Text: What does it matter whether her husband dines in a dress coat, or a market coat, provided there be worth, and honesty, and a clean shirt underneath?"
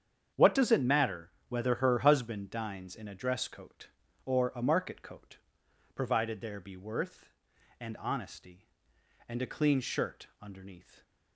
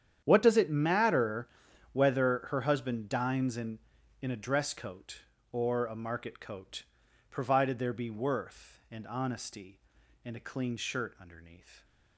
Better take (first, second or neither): first